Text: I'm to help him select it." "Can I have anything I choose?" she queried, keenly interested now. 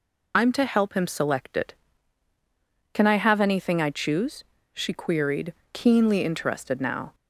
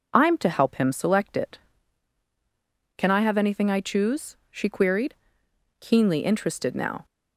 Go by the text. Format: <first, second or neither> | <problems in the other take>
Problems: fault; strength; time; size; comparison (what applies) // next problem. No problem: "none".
second | loses the start of "I'm"; at 0.3 s; 45 ms